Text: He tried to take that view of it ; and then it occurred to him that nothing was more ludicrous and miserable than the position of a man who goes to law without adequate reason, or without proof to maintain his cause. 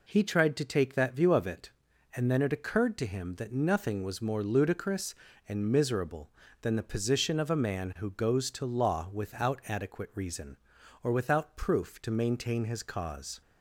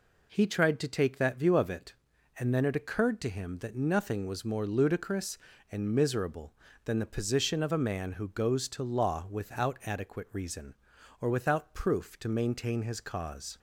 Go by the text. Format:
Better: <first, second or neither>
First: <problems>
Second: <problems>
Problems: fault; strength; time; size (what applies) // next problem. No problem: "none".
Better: neither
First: none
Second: none